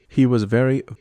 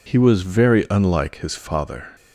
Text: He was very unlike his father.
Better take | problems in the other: second | stops before "unlike his father"; at 0.9 s

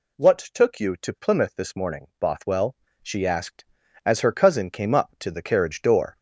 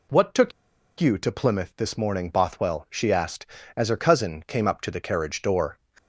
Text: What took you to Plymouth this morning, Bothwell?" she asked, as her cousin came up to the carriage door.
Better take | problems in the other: first | pauses between "took" and "you"; noticeable; at 0.5 s; 0.48 s long

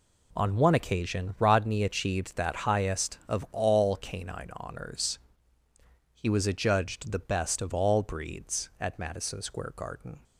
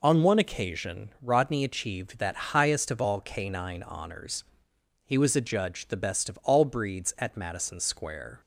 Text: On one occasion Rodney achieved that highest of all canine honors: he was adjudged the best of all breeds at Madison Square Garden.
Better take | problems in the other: first | stops before "Garden"; at 8.4 s

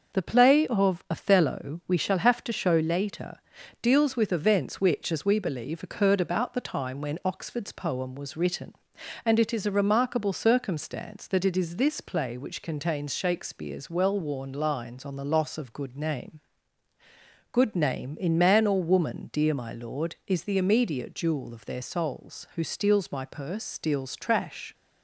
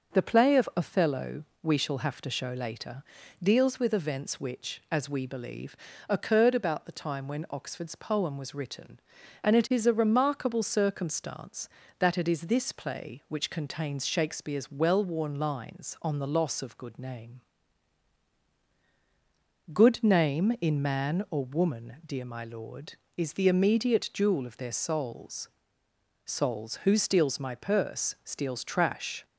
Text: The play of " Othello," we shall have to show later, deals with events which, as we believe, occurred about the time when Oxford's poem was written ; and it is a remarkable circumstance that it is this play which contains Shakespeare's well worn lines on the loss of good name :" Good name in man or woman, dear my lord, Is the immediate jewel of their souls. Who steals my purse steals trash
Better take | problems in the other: first | starts louder than the rest; noticeable; until 1.1 s; 6 dB; noticeable in the first // says "souls" twice; at 26.2 s

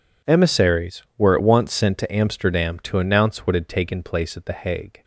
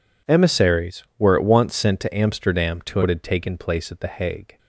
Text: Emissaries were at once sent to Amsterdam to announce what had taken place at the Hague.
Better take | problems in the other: first | skips "announce"; at 3.0 s

